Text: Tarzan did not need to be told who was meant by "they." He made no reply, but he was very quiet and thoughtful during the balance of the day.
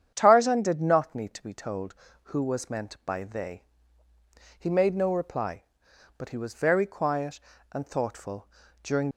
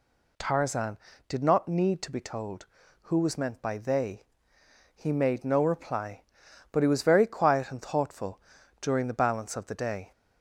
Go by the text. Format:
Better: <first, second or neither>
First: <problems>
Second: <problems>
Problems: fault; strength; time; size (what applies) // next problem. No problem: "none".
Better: second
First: starts louder than the rest; strong; until 1.1 s; 8.5 dB // pauses between "thoughtful" and "during"; slight; at 8.4 s; 0.36 s long // stops before "the balance of the day"; at 9.1 s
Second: pauses between "thoughtful" and "during"; at 8.4 s; 0.40 s long